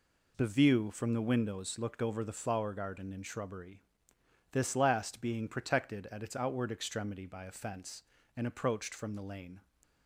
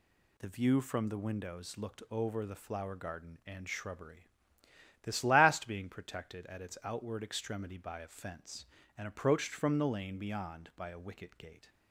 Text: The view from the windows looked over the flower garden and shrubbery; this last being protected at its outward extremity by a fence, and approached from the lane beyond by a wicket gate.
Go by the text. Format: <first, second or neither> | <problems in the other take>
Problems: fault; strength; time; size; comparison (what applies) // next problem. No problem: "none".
second | stops before "beyond by a wicket gate"; at 9.8 s